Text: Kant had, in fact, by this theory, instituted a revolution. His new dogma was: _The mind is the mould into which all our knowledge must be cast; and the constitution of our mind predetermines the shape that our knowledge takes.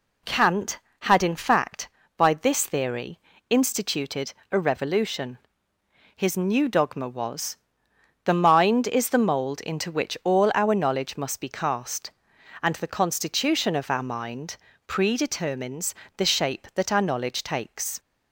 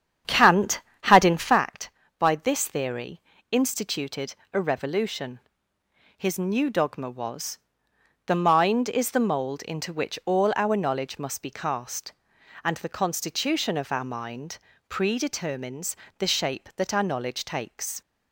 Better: first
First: pauses between "instituted" and "a"; slight; at 4.3 s; 0.18 s long // pauses between "mind" and "predetermines"; slight; at 14.5 s; 0.32 s long // pauses between "predetermines" and "the"; slight; at 15.9 s; 0.22 s long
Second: starts louder than the rest; strong; until 1.7 s; 8.5 dB // pauses between "instituted" and "a"; slight; at 4.3 s; 0.18 s long // pauses between "mind" and "predetermines"; slight; at 14.5 s; 0.32 s long // pauses between "predetermines" and "the"; slight; at 15.9 s; 0.22 s long

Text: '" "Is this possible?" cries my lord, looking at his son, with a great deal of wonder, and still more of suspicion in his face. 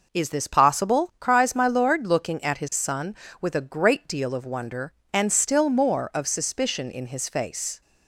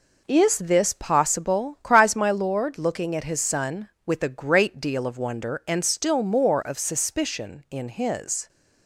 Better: first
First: none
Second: stops before "face"; at 8.4 s

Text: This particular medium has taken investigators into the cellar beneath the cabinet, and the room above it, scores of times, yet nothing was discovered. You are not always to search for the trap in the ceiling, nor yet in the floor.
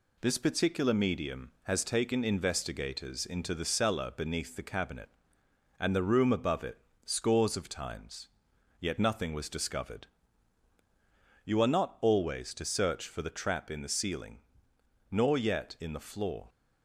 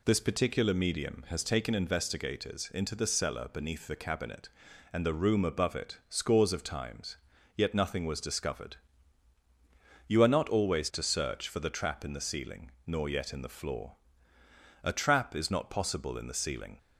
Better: first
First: none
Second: goes on to say "A trap is not possible in the ceiling"; strong; from 14.8 s on; 1.9 s long

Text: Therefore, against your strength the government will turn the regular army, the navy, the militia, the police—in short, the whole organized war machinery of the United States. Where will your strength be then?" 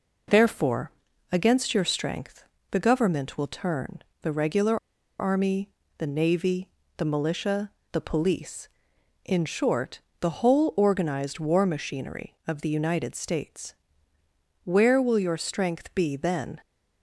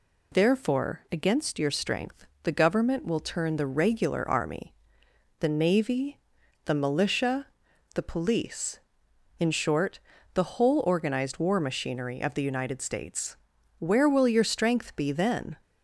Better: second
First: pauses between "strength" and "the"; slight; at 2.4 s; 0.28 s long // pauses between "turn" and "the"; slight; at 4.0 s; 0.18 s long // pauses between "regular" and "army"; at 4.7 s; 0.42 s long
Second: pauses between "strength" and "the"; slight; at 2.2 s; 0.18 s long

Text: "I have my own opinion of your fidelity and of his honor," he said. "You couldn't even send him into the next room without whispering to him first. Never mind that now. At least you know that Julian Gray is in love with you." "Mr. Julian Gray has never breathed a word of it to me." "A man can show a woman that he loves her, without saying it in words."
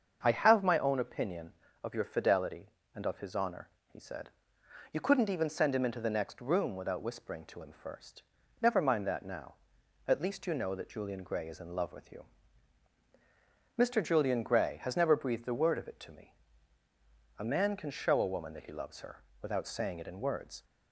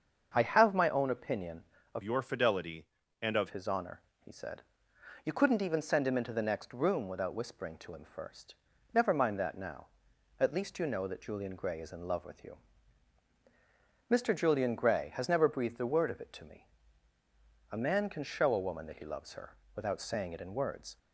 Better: first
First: starts louder than the rest; until 1.2 s; 7 dB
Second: starts louder than the rest; until 1.3 s; 7 dB // changes voice from "your" to "of"; from 2.0 to 3.5 s; 1.5 s long

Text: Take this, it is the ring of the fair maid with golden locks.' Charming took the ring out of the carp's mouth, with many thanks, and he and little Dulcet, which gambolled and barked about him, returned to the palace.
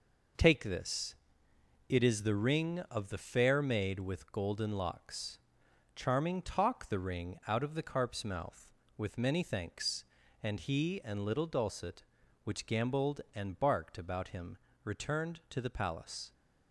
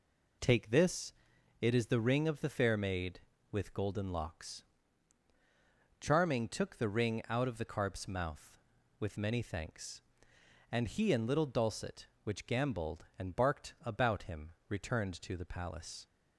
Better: second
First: says "talk" for "took"; at 6.4 s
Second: none

